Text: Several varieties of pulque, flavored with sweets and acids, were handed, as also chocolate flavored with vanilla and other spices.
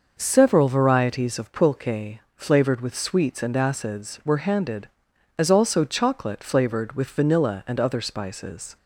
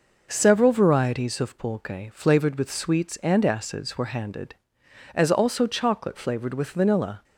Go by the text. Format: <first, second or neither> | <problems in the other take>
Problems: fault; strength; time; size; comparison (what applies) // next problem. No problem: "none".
first | stops before "and other spices"; at 7.2 s